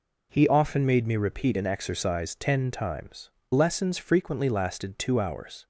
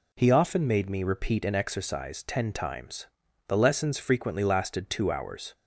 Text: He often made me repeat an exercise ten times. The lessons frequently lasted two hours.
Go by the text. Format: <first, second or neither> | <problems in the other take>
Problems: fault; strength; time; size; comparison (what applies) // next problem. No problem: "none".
second | skips "The"; at 3.4 s